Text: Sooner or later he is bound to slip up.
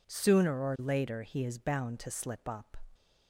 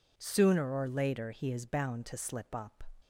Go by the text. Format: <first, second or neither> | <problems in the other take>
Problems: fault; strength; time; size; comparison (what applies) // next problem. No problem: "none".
neither | none